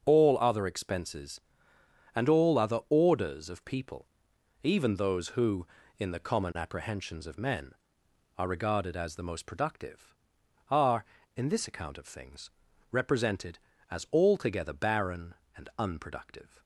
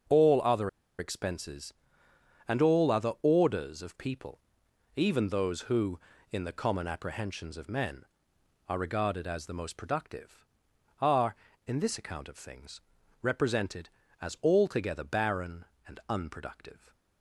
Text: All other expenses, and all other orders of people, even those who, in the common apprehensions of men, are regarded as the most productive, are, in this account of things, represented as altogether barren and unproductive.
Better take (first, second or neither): first